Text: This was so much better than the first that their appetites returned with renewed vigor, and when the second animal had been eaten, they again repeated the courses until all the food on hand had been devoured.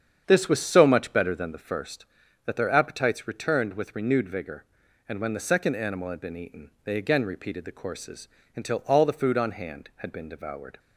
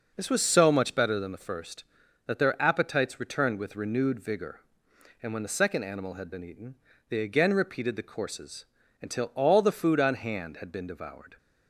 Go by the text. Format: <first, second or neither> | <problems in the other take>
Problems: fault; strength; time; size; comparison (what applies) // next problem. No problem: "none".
second | starts louder than the rest; strong; until 1.9 s; 8 dB // pauses between "courses" and "until"; slight; at 8.2 s; 0.26 s long; slight in the second